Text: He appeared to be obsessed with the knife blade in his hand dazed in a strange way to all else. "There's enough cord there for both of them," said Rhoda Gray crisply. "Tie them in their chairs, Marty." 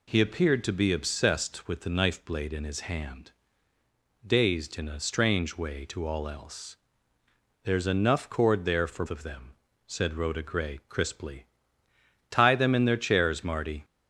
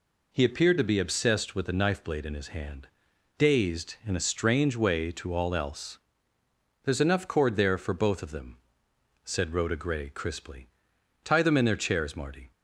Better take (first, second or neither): second